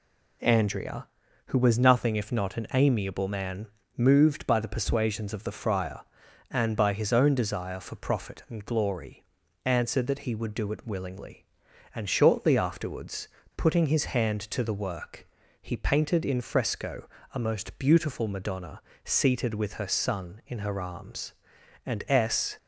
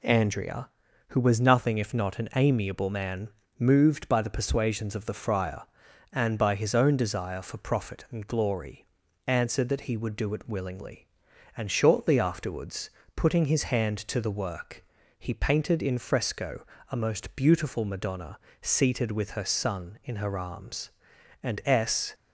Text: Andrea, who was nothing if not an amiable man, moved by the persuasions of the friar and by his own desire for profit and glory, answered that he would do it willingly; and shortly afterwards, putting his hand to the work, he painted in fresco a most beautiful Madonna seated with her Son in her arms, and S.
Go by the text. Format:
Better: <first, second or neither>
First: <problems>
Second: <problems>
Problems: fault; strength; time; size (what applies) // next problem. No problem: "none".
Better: neither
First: pauses between "fresco" and "a"; slight; at 17.0 s; 0.26 s long // pauses between "Madonna" and "seated"; slight; at 18.8 s; 0.24 s long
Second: pauses between "fresco" and "a"; slight; at 16.6 s; 0.26 s long // pauses between "Madonna" and "seated"; slight; at 18.3 s; 0.24 s long